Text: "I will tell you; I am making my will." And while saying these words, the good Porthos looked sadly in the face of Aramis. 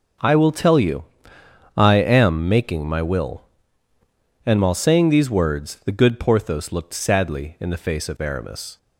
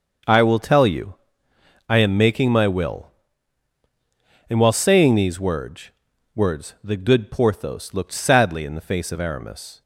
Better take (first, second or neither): first